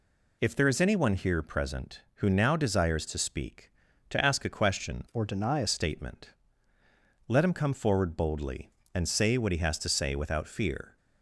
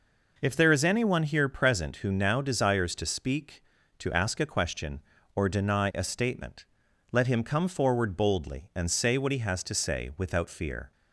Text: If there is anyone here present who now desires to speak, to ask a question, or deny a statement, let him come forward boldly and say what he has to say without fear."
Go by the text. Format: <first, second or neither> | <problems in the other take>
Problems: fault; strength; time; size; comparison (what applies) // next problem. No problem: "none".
second | changes voice from "or" to "a"; from 5.1 to 5.6 s; 0.5 s long